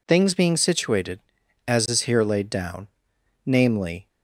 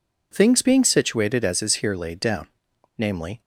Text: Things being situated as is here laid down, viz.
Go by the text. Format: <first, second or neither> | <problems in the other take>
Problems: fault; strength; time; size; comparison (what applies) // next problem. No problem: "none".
neither | none